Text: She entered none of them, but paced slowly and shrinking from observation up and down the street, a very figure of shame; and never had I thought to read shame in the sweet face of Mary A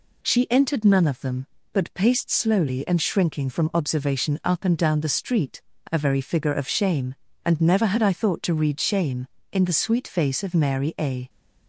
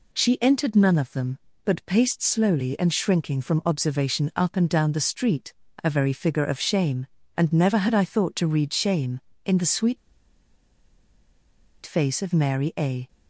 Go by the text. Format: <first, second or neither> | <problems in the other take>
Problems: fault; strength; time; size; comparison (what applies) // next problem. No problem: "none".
first | pauses between "sweet" and "face"; strong; at 9.9 s; 1.8 s long